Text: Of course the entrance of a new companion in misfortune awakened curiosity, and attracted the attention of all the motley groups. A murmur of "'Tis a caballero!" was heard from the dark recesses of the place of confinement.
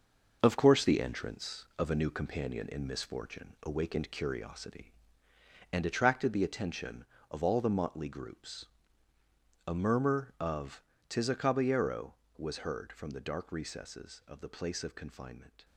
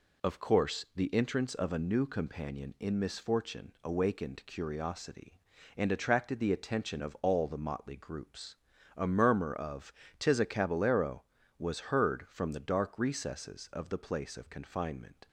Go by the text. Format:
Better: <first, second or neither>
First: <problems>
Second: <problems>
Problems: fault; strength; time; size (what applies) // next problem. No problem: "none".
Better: second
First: gets quieter; strong; throughout; 8 dB // pauses between "of" and "Tis"; slight; at 10.8 s; 0.28 s long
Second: pauses between "of" and "Tis"; slight; at 9.9 s; 0.26 s long